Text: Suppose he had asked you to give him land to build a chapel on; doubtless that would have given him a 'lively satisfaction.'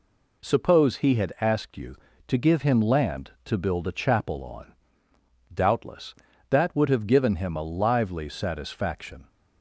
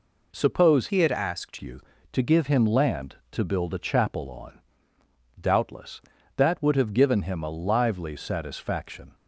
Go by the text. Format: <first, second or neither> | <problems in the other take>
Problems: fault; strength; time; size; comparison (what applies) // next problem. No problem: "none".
first | changes voice from "he" to "asked"; from 0.8 to 1.5 s; 0.7 s long